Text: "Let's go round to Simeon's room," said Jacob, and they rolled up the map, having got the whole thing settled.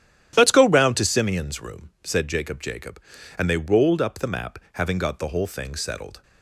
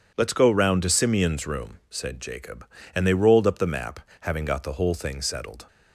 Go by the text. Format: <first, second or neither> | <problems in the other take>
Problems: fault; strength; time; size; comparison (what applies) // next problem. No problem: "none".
second | starts louder than the rest; strong; until 1.3 s; 11 dB // says "Jacob" twice; at 2.6 s